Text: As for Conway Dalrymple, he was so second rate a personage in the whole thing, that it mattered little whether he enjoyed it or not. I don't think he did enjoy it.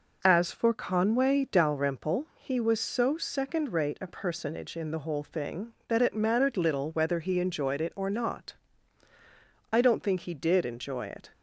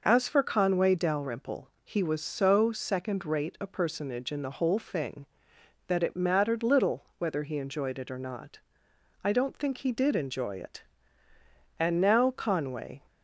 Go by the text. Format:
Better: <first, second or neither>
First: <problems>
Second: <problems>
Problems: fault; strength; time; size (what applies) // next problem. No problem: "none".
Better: first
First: none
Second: goes on to say "And now Conway"; noticeable; from 11.7 s on; 1.2 s long